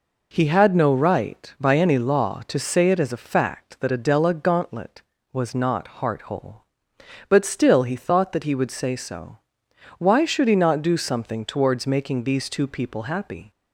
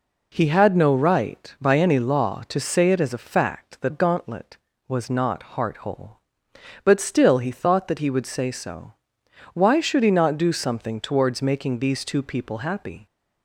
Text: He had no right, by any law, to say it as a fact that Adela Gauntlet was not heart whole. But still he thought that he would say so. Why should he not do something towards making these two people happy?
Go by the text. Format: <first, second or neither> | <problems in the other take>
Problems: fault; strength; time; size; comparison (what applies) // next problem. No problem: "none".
first | skips "Adela"; at 3.9 s